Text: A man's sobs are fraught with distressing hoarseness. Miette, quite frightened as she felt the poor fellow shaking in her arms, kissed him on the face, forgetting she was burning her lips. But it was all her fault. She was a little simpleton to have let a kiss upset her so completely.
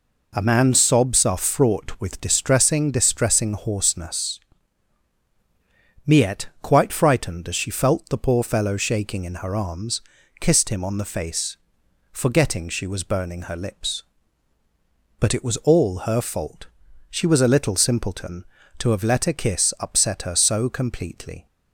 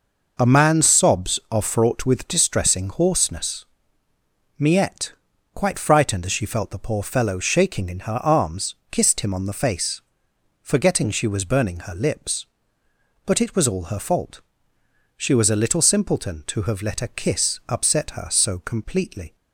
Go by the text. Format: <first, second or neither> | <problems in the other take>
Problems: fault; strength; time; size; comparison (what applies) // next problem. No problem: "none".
second | says "distressing" twice; at 2.8 s